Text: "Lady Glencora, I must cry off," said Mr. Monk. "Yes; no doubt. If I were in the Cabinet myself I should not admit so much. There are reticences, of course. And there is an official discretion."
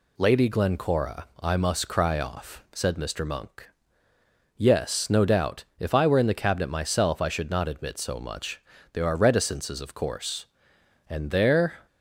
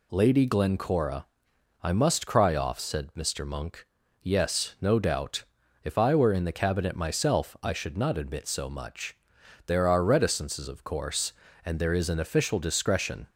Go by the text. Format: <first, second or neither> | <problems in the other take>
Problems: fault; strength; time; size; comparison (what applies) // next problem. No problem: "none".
second | stops before "is an official discretion"; at 11.8 s